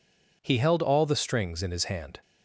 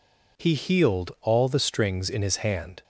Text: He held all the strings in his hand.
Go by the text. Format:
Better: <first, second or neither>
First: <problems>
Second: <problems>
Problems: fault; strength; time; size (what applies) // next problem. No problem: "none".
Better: first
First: none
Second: says "healed" for "held"; at 0.5 s